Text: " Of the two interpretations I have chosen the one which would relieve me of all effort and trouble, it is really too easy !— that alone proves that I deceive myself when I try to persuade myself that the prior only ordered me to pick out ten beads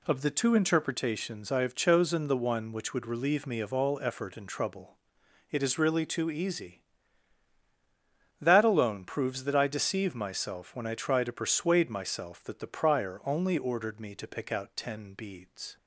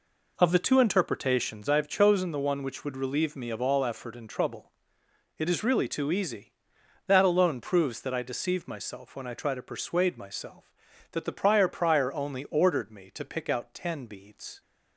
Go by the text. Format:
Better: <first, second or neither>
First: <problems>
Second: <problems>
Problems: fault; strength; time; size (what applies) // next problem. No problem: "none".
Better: first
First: none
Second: says "prior" twice; at 11.6 s